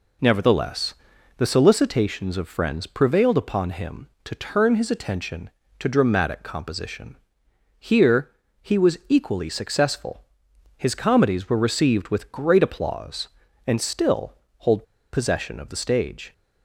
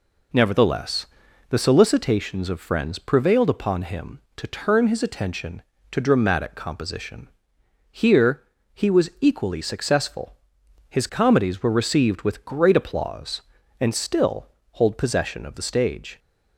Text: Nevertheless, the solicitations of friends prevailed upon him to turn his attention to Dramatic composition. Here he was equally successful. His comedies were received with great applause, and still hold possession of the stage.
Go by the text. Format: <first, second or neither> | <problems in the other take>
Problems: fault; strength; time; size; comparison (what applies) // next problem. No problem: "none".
second | pauses between "Here" and "he"; slight; at 8.3 s; 0.30 s long; slight in the second // pauses between "still" and "hold"; slight; at 14.3 s; 0.26 s long; slight in the second // pauses between "hold" and "possession"; slight; at 14.8 s; 0.27 s long